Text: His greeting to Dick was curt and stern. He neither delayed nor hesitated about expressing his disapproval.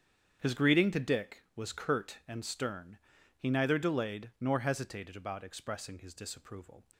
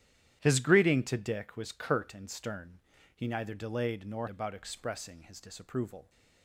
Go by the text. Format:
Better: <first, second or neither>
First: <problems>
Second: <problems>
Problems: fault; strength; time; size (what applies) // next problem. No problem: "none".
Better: first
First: starts louder than the rest; strong; until 1.4 s; 8.5 dB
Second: starts louder than the rest; strong; until 1.4 s; 11 dB // skips "hesitated"; at 4.2 s